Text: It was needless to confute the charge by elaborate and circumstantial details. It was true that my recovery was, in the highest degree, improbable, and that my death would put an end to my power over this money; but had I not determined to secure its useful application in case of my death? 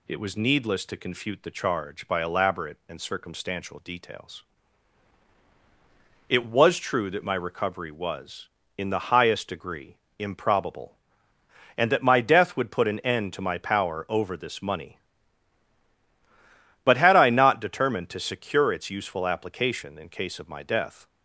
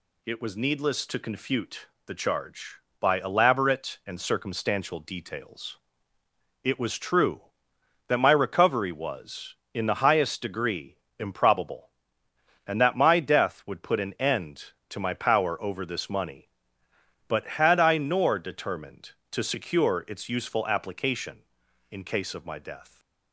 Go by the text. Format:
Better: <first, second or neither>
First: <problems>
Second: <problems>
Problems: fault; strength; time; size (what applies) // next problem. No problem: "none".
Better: first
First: none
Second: pauses between "confute" and "the"; slight; at 1.8 s; 0.18 s long // says "nor" for "not"; at 17.9 s